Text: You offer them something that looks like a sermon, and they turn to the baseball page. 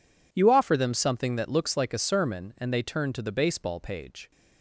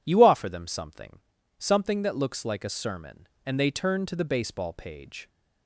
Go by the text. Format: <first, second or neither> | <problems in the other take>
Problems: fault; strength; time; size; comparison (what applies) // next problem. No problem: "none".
first | says "something" twice; at 1.5 s